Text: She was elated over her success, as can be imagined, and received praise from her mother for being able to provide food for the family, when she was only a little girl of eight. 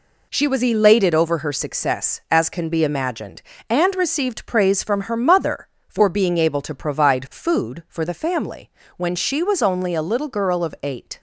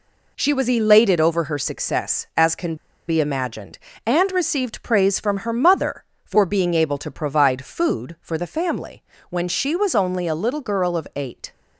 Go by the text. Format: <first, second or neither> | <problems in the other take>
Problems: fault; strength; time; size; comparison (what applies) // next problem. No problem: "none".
first | pauses between "can" and "be"; slight; at 2.7 s; 0.32 s long